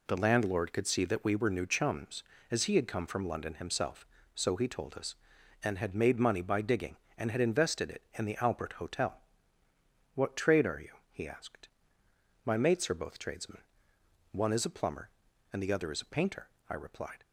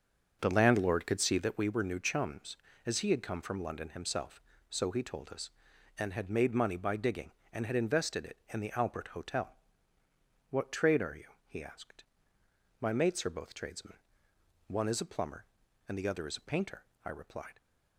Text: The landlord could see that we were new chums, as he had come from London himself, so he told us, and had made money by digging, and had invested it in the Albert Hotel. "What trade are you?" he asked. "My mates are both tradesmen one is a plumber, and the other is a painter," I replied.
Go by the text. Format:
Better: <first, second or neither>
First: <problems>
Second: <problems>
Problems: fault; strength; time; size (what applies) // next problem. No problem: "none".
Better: first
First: pauses between "tradesmen" and "one"; noticeable; at 13.6 s; 0.68 s long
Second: starts louder than the rest; until 1.6 s; 7 dB // pauses between "tradesmen" and "one"; noticeable; at 13.9 s; 0.68 s long